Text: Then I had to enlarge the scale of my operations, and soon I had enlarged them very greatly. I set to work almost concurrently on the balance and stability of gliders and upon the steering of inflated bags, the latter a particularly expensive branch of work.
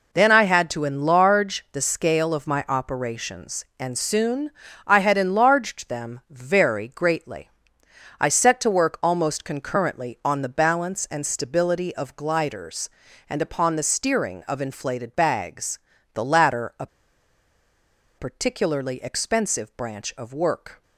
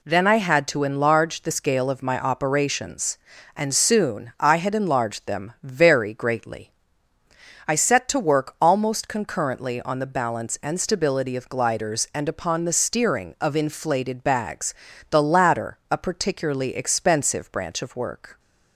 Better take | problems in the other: second | pauses between "soon" and "I"; slight; at 4.5 s; 0.34 s long // pauses between "a" and "particularly"; strong; at 16.8 s; 1.3 s long

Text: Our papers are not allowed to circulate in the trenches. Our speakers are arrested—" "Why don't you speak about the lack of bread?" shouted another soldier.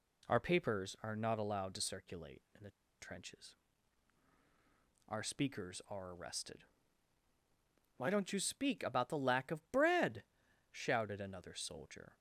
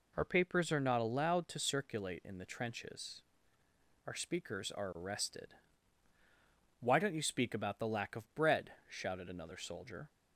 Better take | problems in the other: second | pauses between "the" and "trenches"; slight; at 2.6 s; 0.29 s long

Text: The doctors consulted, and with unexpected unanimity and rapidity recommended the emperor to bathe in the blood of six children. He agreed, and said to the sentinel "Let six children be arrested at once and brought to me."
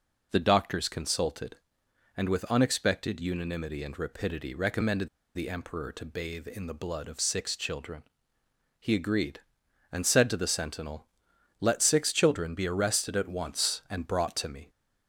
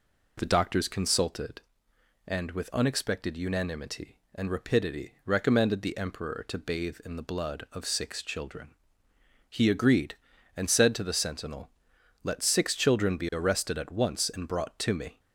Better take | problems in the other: second | pauses between "recommended" and "the"; slight; at 5.0 s; 0.27 s long // pauses between "sentinel" and "Let"; noticeable; at 11.0 s; 0.52 s long; noticeable in the second

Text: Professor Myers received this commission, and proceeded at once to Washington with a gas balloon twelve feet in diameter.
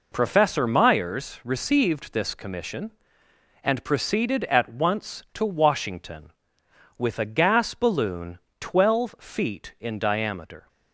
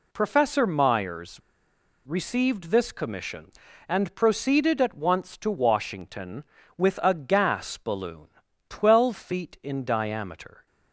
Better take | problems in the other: first | pauses between "Myers" and "received"; noticeable; at 1.3 s; 0.66 s long // pauses between "balloon" and "twelve"; at 8.2 s; 0.40 s long; slight in the first

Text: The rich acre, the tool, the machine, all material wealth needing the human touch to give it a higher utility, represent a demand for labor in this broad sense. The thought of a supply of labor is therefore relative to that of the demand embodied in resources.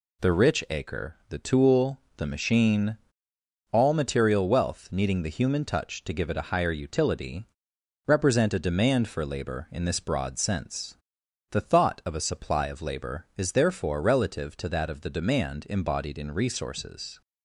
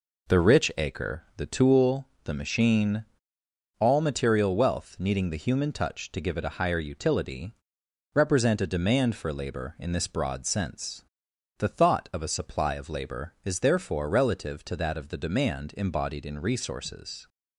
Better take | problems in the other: first | starts louder than the rest; noticeable; until 1.8 s; 4 dB

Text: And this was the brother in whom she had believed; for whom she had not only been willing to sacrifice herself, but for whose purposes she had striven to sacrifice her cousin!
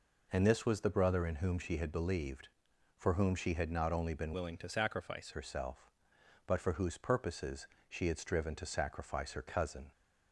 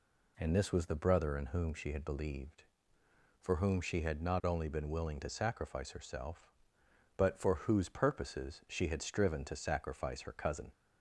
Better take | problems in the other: second | changes voice from "willing" to "sacrifice"; from 4.3 to 5.3 s; 1.0 s long // pauses between "purposes" and "she"; slight; at 7.6 s; 0.20 s long

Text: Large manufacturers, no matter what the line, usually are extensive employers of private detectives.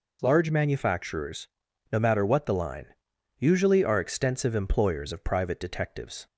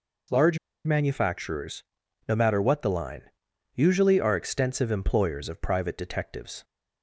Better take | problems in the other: first | pauses between "Large" and "manufacturers"; slight; at 0.5 s; 0.27 s long

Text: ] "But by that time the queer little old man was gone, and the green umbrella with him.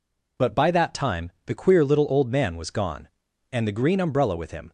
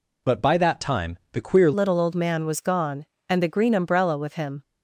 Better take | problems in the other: first | changes voice at "little"; from 1.7 s on; 2.9 s long

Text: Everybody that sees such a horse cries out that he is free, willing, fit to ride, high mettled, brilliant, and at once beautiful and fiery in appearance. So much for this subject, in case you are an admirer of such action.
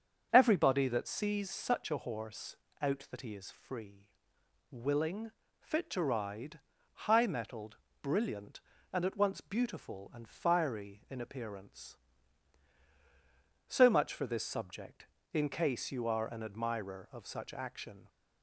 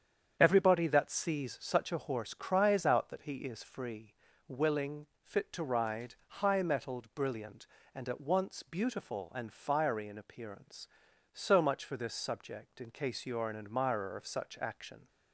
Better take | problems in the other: second | starts louder than the rest; until 1.3 s; 7 dB; strong in the second // skips "cries"; at 2.6 s

